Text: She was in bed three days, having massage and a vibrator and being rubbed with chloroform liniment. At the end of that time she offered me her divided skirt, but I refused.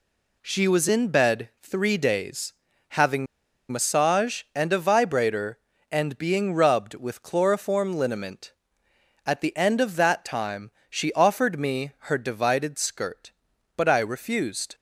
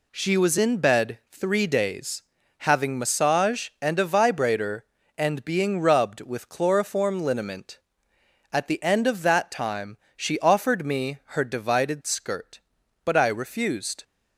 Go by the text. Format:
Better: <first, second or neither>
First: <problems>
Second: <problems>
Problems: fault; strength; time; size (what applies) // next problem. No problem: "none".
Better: second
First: pauses between "having" and "massage"; at 3.2 s; 0.44 s long // pauses between "time" and "she"; slight; at 10.7 s; 0.18 s long // pauses between "me" and "her"; slight; at 11.9 s; 0.16 s long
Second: pauses between "time" and "she"; slight; at 9.9 s; 0.18 s long // pauses between "me" and "her"; slight; at 11.1 s; 0.16 s long